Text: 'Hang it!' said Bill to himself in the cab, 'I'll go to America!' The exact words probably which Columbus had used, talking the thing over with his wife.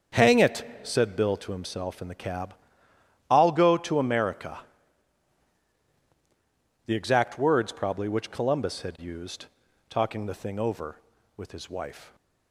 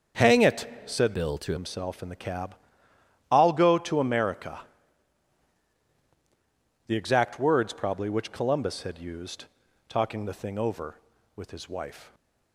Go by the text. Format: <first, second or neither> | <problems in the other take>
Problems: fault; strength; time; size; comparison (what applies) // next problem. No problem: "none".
first | starts louder than the rest; until 1.3 s; 7 dB; also in the first // changes voice from "Bill" to "to"; from 1.1 to 1.5 s; 0.4 s long